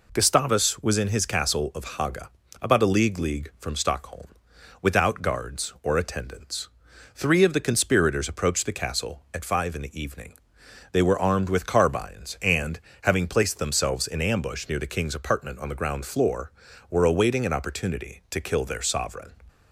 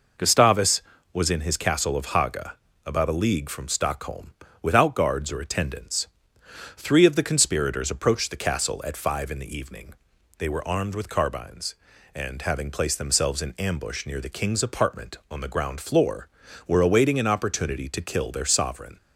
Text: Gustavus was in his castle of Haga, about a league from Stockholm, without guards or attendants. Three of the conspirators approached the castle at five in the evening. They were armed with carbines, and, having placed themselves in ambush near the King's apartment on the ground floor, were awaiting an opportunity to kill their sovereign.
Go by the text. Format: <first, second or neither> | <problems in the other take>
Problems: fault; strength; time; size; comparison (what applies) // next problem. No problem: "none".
second | says "league" twice; at 3.1 s